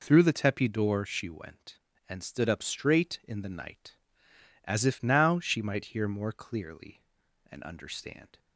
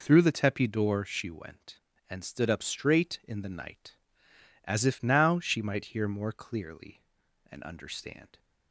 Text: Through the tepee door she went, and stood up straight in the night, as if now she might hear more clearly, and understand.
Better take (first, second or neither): neither